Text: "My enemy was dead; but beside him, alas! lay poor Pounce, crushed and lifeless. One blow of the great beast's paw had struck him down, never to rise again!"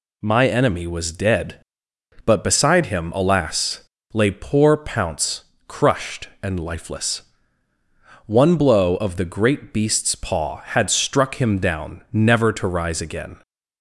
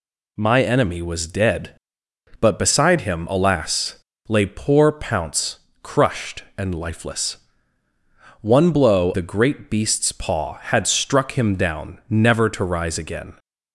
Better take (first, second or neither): first